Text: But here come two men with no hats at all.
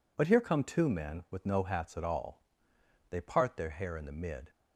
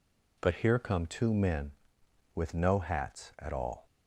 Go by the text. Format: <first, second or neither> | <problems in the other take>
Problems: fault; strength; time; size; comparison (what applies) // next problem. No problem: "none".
second | goes on to say "They part their hair in the mid"; from 3.0 s on; 1.4 s long